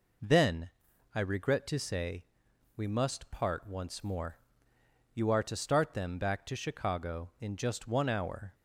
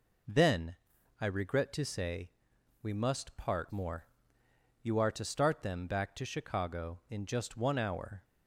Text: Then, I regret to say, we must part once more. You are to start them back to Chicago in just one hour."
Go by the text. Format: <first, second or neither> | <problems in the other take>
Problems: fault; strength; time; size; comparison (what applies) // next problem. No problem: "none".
first | skips "once"; at 3.7 s